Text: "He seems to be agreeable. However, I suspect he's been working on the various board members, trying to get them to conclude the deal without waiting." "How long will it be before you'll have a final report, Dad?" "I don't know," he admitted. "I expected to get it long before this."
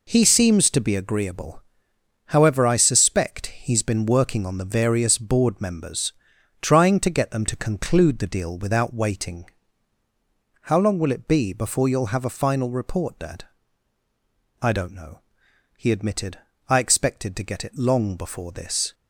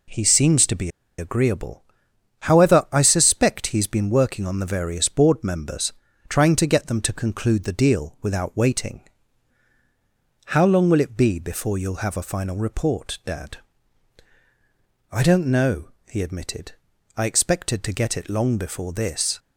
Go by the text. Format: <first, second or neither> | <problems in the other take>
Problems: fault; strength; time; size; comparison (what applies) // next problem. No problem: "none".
first | pauses between "be" and "agreeable"; slight; at 0.8 s; 0.29 s long